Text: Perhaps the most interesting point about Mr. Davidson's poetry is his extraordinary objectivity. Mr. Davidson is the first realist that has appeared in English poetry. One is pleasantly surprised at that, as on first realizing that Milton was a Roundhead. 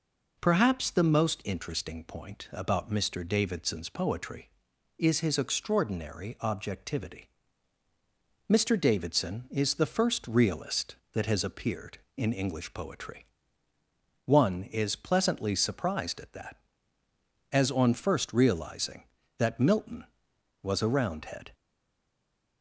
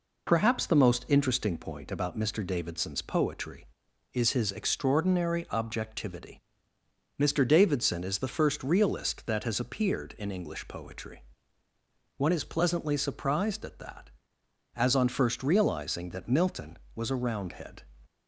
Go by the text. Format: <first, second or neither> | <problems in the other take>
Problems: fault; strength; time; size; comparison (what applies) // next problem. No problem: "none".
second | stays silent after the last word; from 21.5 s on; 1.1 s long